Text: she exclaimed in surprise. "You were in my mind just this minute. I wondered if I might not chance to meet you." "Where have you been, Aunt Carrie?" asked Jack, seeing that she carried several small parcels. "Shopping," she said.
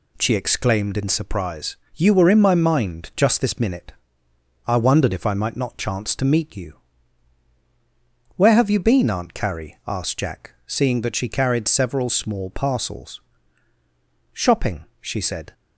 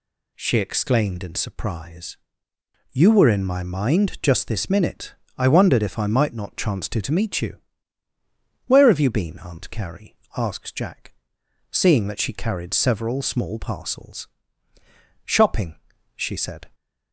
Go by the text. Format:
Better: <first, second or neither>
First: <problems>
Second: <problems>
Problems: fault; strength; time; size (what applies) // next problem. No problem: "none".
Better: first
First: none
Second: says "to" twice; at 7.0 s